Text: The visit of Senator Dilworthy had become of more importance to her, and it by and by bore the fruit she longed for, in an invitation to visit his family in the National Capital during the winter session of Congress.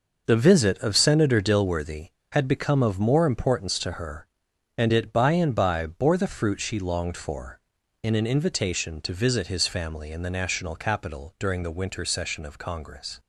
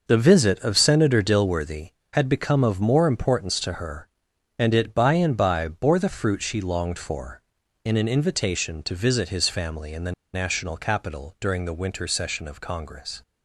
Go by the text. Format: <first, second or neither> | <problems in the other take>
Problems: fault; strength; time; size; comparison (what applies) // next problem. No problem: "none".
first | pauses between "the" and "National"; slight; at 10.1 s; 0.21 s long